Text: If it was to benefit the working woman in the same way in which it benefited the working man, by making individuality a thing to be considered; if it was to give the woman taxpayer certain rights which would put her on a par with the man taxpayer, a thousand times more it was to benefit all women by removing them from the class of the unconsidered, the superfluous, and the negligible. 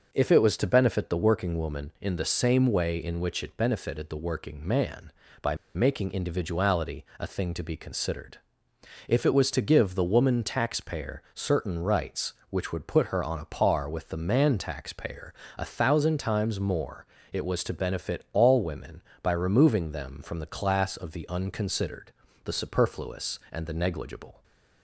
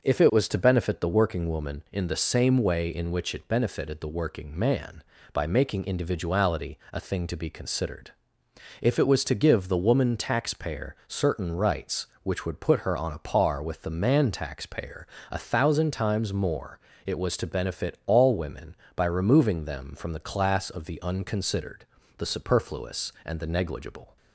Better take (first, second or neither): second